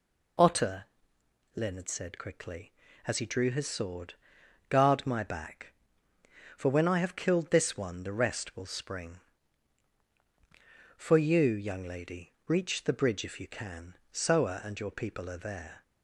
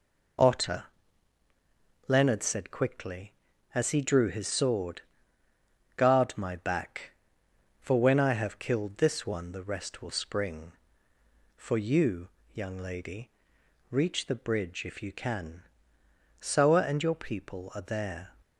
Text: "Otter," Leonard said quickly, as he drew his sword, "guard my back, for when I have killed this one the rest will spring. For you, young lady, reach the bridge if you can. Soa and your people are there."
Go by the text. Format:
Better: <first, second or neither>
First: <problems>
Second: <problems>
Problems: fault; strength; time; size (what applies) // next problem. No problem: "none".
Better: neither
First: none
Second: none